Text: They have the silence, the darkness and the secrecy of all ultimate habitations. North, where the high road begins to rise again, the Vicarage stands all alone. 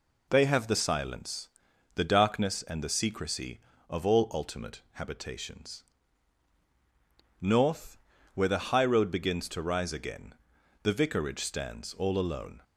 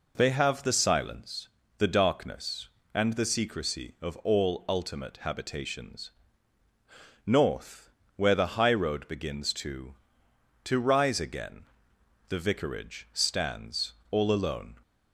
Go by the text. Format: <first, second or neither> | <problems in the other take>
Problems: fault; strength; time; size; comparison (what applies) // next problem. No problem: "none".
first | says "to" twice; at 10.6 s // pauses between "stands" and "all"; slight; at 13.9 s; 0.17 s long